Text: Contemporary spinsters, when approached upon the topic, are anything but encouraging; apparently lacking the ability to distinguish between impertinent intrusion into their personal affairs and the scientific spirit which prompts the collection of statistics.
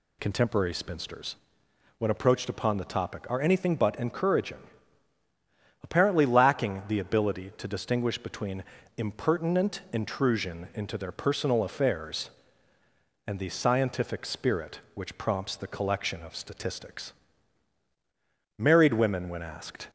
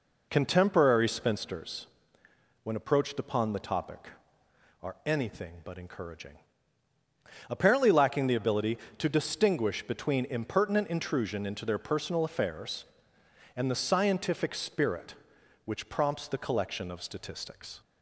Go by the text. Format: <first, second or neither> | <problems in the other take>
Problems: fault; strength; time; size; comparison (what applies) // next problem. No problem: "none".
second | pauses between "between" and "impertinent"; slight; at 8.6 s; 0.36 s long // goes on to say "Married women when asked"; noticeable; from 18.5 s on; 1.3 s long